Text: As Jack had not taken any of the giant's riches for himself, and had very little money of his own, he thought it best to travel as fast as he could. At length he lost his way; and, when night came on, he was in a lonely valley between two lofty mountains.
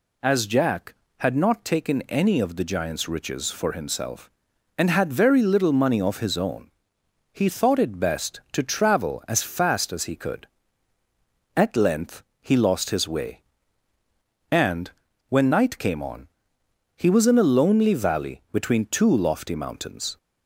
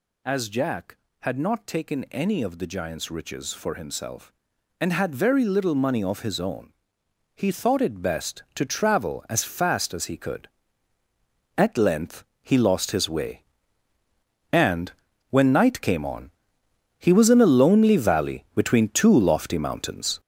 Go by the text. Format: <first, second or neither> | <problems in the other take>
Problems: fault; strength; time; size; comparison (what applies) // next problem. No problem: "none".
first | gets louder; strong; throughout; 8 dB // pauses between "length" and "he"; slight; at 12.2 s; 0.18 s long; slight in the first